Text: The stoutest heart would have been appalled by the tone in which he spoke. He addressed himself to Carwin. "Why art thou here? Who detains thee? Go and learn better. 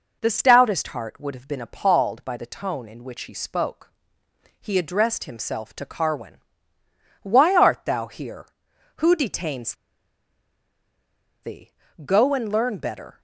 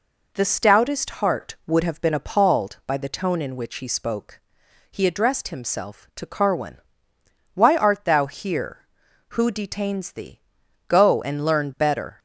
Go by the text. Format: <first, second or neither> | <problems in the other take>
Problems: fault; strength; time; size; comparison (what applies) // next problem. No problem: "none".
second | pauses between "detains" and "thee"; strong; at 9.7 s; 1.6 s long